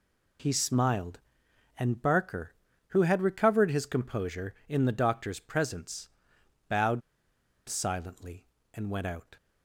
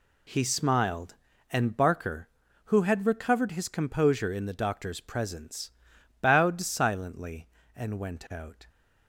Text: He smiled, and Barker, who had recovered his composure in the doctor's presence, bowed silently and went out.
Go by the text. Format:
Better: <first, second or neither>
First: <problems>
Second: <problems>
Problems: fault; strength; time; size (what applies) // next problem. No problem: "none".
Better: second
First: pauses between "bowed" and "silently"; noticeable; at 7.0 s; 0.67 s long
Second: none